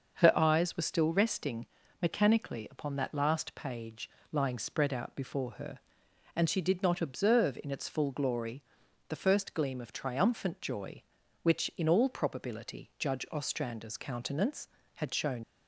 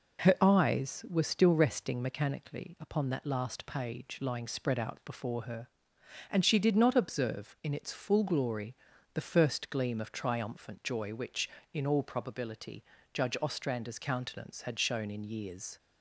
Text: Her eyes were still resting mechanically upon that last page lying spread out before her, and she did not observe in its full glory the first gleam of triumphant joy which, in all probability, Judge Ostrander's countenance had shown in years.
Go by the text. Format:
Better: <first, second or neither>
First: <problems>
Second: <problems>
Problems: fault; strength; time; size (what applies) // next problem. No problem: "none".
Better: second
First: starts louder than the rest; until 1.2 s; 6.5 dB // pauses between "resting" and "mechanically"; slight; at 1.6 s; 0.34 s long // pauses between "page" and "lying"; slight; at 4.0 s; 0.22 s long // pauses between "glory" and "the"; noticeable; at 8.6 s; 0.46 s long // stops before "in years"; at 15.4 s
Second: pauses between "glory" and "the"; at 8.7 s; 0.38 s long